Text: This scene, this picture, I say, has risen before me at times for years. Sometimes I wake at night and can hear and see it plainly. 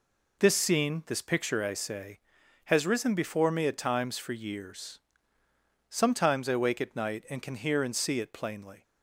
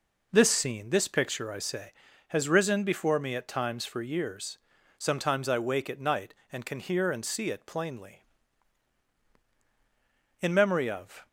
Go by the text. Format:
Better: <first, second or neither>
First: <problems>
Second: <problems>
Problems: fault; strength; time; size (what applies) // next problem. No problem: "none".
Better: first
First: none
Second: goes on to say "IN MEMORY OF"; noticeable; from 10.3 s on; 0.88 s long